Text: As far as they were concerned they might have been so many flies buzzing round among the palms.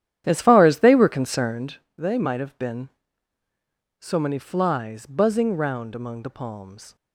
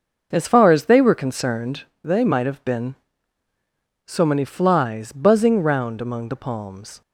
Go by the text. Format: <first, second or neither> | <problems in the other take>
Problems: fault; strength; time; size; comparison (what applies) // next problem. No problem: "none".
second | starts louder than the rest; strong; until 1.7 s; 10.5 dB // pauses between "concerned" and "they"; slight; at 1.7 s; 0.22 s long; slight in the second